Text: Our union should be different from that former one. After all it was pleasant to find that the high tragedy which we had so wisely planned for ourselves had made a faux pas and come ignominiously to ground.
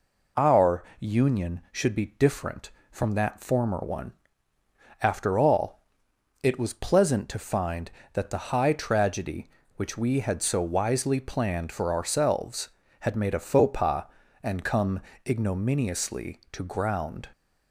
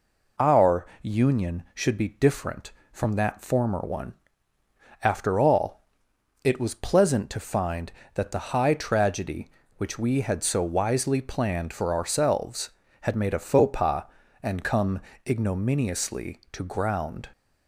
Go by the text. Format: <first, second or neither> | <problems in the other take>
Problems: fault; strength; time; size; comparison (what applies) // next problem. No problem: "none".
neither | pauses between "Our" and "union"; slight; the same in both // pauses between "all" and "it"; noticeable; the same in both // pauses between "come" and "ignominiously"; slight; the same in both